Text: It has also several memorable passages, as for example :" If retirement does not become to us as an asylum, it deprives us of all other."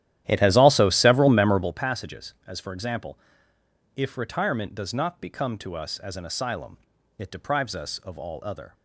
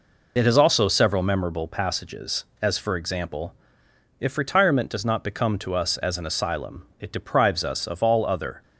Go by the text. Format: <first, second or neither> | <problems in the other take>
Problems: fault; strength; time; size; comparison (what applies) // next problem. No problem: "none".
second | starts louder than the rest; strong; until 1.8 s; 12.5 dB